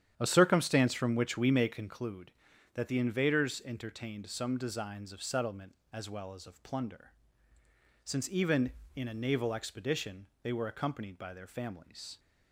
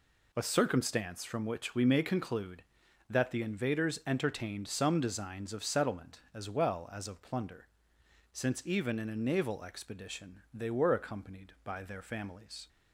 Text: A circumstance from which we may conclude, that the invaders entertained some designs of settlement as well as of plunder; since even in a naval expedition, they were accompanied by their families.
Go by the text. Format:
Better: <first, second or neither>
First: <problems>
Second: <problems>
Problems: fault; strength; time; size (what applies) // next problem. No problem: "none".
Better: second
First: starts louder than the rest; strong; until 2.0 s; 9.5 dB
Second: none